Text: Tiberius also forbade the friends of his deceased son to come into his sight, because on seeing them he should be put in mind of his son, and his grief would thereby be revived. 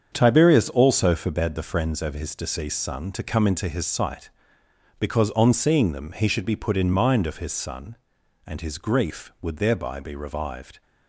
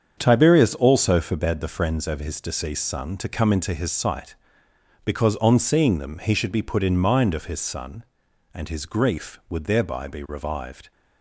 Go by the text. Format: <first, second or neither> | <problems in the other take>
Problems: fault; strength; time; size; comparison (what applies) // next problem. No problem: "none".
neither | starts louder than the rest; strong; the same in both